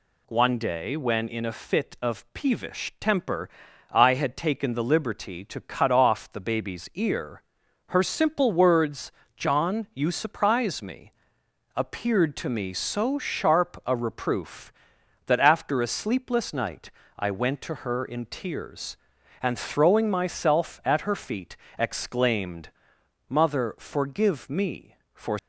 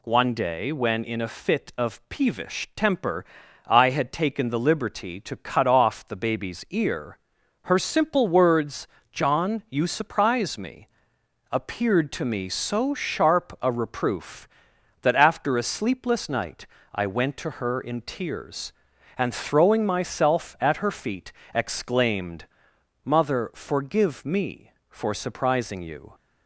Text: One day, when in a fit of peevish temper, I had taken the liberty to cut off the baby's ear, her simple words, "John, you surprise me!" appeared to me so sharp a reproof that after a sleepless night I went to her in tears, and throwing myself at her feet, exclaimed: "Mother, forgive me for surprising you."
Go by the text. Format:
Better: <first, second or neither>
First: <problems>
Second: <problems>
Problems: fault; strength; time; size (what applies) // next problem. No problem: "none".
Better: second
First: pauses between "night" and "I"; slight; at 16.8 s; 0.30 s long // stops before "surprising you"; at 25.3 s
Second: pauses between "night" and "I"; slight; at 16.6 s; 0.30 s long